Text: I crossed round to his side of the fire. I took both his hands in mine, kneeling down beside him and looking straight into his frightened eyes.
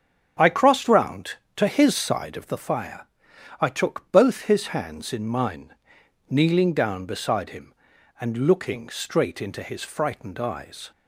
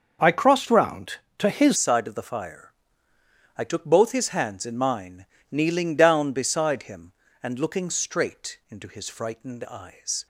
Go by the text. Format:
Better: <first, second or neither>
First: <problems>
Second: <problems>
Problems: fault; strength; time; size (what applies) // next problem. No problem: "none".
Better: first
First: starts louder than the rest; strong; until 1.6 s; 8 dB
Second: starts louder than the rest; until 1.4 s; 6.5 dB // changes voice at "side"; from 1.7 s on; 8.5 s long